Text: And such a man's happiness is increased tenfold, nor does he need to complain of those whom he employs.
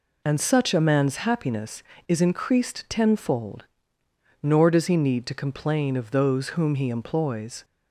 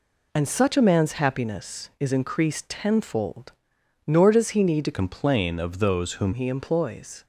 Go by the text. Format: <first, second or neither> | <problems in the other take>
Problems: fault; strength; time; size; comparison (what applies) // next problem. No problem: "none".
first | changes voice from "complain" to "whom"; from 4.9 to 6.3 s; 1.4 s long